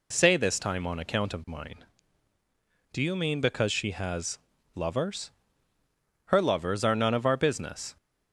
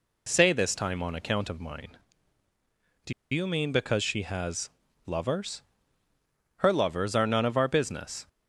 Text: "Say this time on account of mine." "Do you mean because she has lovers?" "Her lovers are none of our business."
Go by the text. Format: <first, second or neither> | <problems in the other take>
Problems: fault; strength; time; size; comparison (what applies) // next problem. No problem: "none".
first | pauses between "Do" and "you"; slight; at 3.1 s; 0.20 s long // pauses between "has" and "lovers"; slight; at 4.6 s; 0.34 s long; slight in the first